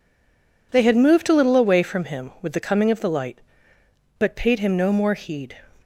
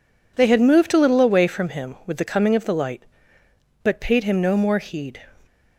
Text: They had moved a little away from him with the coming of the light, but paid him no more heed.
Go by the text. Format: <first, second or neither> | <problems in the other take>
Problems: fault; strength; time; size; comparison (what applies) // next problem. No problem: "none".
second | stays silent before the first word; slight; until 0.7 s; 0.7 s long